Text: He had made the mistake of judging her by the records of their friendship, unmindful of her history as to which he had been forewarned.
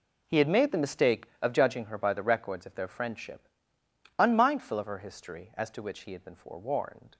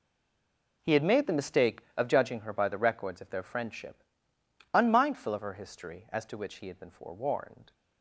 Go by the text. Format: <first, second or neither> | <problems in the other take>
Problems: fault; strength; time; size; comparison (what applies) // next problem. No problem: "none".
first | stays silent before the first word; slight; until 0.8 s; 0.8 s long